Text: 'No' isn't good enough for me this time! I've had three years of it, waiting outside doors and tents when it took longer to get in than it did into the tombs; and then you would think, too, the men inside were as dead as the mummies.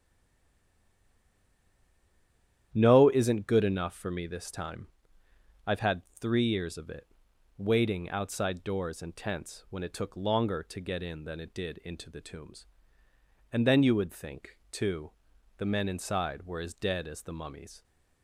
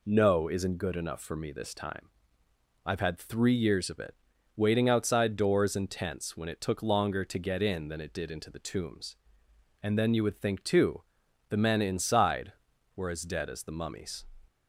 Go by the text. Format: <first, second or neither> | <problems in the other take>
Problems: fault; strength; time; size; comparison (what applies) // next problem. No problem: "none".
second | stays silent before the first word; strong; until 2.7 s; 2.7 s long // starts louder than the rest; strong; until 3.7 s; 10.5 dB // pauses between "had" and "three"; slight; at 6.0 s; 0.18 s long